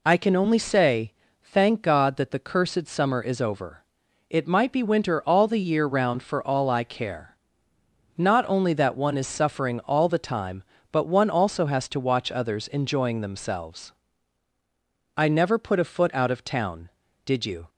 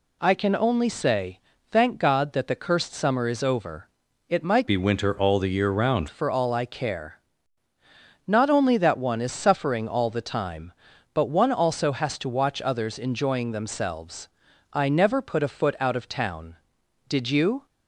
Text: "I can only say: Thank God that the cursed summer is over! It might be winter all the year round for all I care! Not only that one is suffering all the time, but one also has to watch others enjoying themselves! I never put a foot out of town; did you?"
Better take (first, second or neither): first